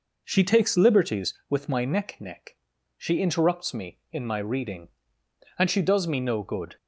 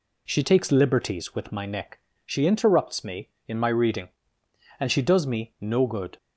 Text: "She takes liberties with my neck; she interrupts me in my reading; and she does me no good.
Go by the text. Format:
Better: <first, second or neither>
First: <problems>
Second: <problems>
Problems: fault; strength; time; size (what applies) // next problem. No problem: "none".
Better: second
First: says "neck" twice; at 2.1 s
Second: none